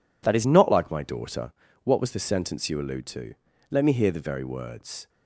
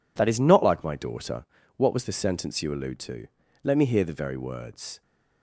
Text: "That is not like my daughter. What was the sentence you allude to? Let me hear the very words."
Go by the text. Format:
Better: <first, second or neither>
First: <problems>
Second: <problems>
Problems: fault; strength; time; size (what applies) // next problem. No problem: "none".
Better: neither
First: none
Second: none